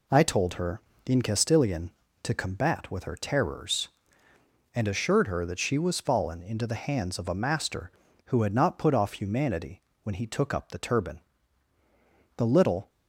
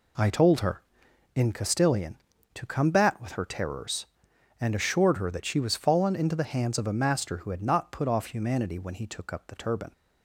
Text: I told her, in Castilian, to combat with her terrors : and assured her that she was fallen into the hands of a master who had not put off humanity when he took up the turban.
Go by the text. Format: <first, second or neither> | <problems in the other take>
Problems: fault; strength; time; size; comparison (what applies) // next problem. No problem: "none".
second | pauses between "humanity" and "when"; slight; at 9.8 s; 0.22 s long // goes on to say "The little"; from 12.3 s on; 0.52 s long